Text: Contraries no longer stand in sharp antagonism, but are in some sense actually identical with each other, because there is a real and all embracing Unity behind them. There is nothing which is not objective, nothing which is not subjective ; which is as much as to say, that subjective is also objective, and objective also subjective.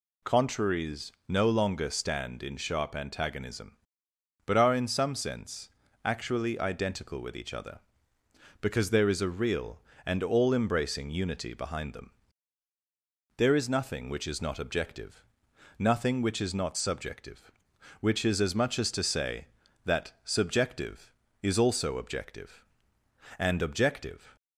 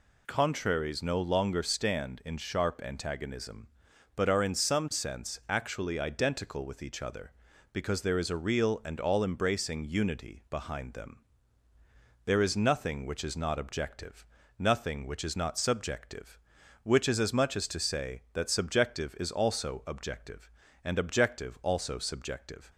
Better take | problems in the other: second | pauses between "Contraries" and "no"; slight; at 1.1 s; 0.16 s long // pauses between "sense" and "actually"; slight; at 5.6 s; 0.36 s long // stops before "also subjective"; at 24.3 s

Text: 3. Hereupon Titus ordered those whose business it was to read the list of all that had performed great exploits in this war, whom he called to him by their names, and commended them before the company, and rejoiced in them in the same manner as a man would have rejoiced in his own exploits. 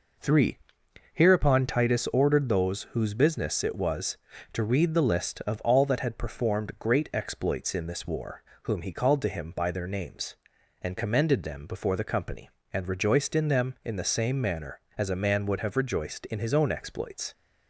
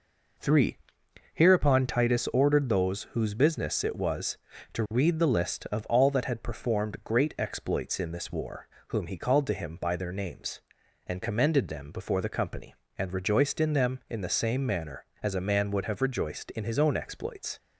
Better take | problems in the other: neither | none

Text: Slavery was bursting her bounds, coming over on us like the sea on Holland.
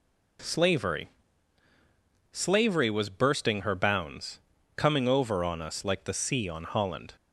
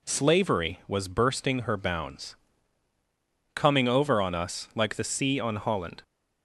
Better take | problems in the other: second | says "Slavery" twice; at 2.3 s

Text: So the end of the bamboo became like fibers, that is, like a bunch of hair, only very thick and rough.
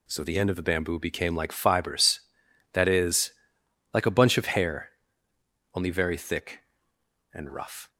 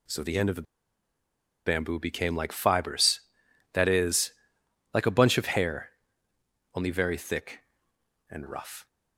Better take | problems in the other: first | pauses between "the" and "bamboo"; at 0.6 s; 1.0 s long

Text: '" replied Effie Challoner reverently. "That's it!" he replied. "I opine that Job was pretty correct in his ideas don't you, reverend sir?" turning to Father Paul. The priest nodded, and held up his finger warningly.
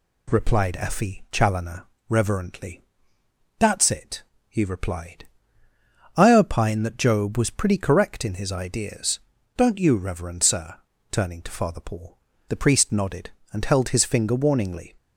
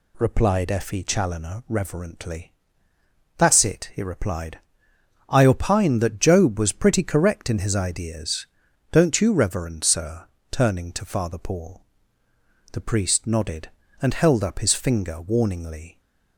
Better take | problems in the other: second | pauses between "Challoner" and "reverently"; slight; at 1.8 s; 0.20 s long // pauses between "ideas" and "don't"; slight; at 9.2 s; 0.36 s long; noticeable in the second // skips "up"; at 13.8 s

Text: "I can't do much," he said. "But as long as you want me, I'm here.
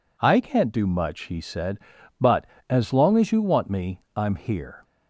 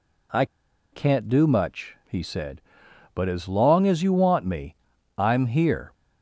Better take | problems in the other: first | pauses between "I" and "can't"; noticeable; at 0.4 s; 0.47 s long

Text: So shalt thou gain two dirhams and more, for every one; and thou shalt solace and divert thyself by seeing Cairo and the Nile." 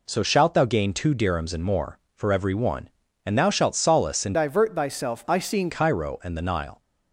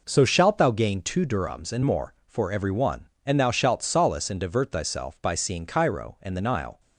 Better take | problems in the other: second | changes voice from "divert" to "seeing"; from 4.3 to 5.6 s; 1.3 s long

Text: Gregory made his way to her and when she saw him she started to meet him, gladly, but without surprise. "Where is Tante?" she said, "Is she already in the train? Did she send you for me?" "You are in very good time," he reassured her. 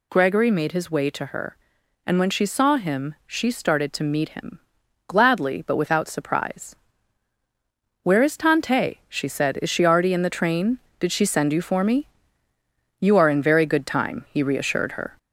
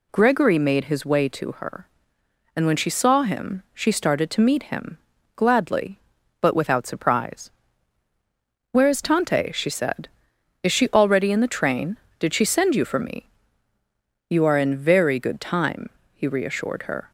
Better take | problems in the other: second | gets louder; slight; throughout; 2.5 dB

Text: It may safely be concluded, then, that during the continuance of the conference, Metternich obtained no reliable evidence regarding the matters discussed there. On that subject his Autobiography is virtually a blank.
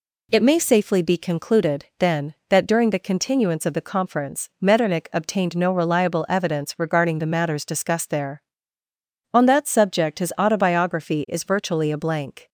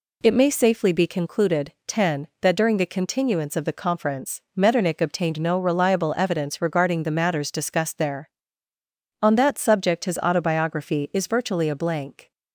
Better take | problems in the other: first | says "ten" for "then"; at 1.8 s

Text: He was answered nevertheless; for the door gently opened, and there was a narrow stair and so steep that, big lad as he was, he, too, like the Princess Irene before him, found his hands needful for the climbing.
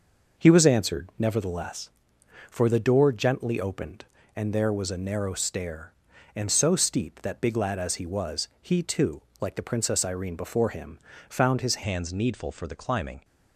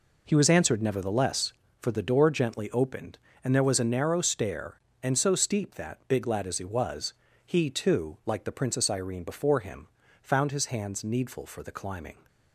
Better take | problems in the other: second | changes voice at "hands"; from 11.8 s on; 1.4 s long

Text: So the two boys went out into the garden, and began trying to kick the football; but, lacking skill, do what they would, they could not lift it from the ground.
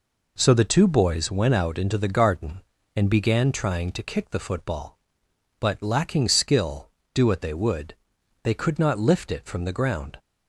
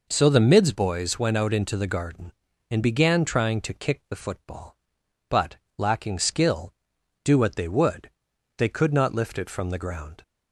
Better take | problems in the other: first | says "mids" for "two"; at 0.3 s

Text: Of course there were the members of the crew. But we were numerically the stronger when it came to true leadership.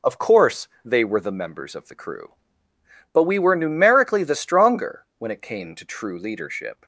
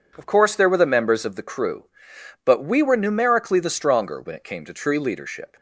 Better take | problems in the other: second | says "they" for "there"; at 0.8 s

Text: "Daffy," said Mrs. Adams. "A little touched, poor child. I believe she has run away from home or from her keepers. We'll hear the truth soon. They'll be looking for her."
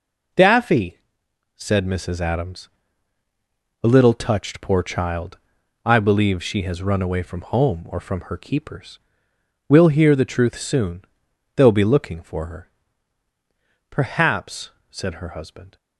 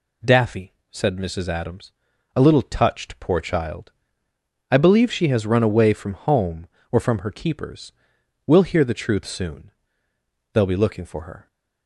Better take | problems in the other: second | goes on to say "Perhaps said her husband"; strong; from 13.8 s on; 1.8 s long

